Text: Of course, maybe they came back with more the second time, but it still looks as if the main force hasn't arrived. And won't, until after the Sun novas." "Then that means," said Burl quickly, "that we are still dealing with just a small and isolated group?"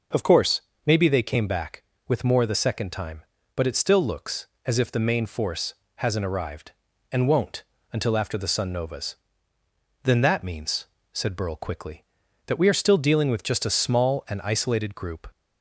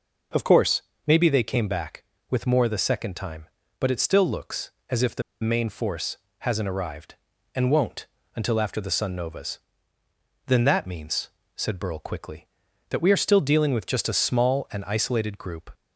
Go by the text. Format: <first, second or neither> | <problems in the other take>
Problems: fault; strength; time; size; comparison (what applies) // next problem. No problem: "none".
first | pauses between "the" and "main"; slight; at 5.2 s; 0.19 s long // pauses between "force" and "hasn't"; slight; at 6.1 s; 0.22 s long; slight in the first